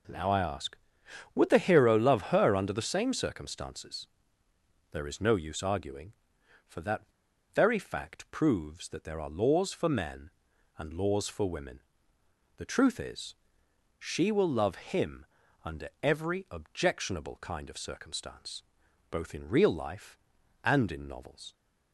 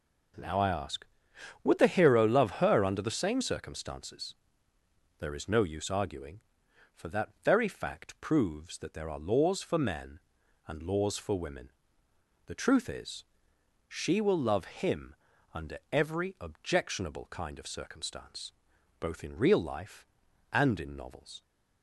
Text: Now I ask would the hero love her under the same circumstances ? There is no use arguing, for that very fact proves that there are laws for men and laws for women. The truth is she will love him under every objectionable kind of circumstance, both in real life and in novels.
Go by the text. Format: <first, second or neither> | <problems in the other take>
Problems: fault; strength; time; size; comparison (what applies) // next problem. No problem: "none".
second | pauses between "that" and "very"; noticeable; at 7.0 s; 0.52 s long // pauses between "is" and "she"; noticeable; at 13.3 s; 0.64 s long; noticeable in the second // pauses between "him" and "under"; at 15.2 s; 0.40 s long; also in the second